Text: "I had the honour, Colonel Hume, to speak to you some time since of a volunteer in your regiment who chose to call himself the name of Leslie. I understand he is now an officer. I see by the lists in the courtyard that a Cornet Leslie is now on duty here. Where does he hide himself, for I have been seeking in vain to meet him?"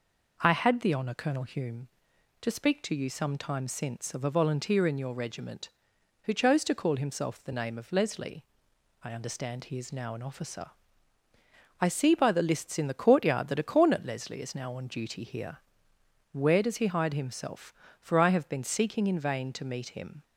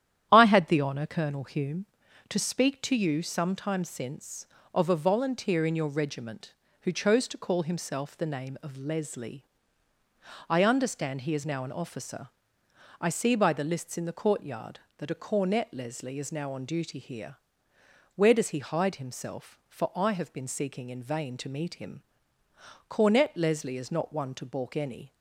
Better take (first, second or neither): first